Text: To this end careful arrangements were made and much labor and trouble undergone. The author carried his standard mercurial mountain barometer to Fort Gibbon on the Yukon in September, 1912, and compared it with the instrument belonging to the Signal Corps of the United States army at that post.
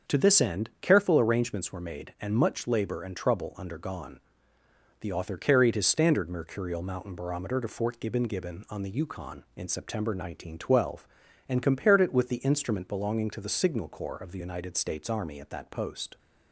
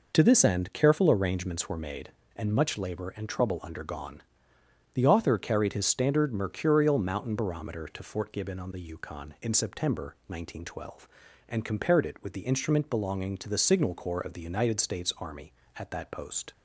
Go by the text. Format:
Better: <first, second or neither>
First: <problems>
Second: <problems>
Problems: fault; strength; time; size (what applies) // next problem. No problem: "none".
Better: second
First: starts louder than the rest; until 1.2 s; 7 dB // says "Gibbon" twice; at 8.2 s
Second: none